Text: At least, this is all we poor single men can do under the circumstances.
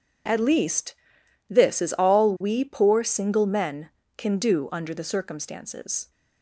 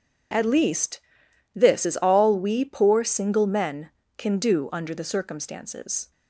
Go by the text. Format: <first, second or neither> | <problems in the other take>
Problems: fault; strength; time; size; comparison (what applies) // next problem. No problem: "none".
neither | none